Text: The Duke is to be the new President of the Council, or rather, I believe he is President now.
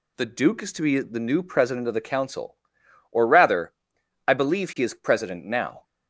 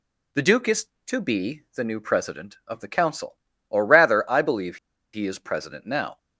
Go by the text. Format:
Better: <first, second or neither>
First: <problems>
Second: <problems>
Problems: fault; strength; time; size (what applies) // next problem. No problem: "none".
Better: first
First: none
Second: pauses between "believe" and "he"; at 4.7 s; 0.36 s long